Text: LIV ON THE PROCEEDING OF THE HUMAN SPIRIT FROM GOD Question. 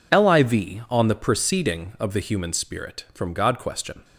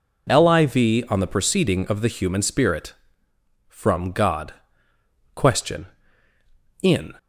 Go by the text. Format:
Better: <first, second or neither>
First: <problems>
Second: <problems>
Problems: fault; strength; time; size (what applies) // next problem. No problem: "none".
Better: first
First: none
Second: pauses between "GOD" and "Question"; noticeable; at 4.5 s; 0.82 s long // goes on to say "In"; slight; from 6.8 s on; 0.30 s long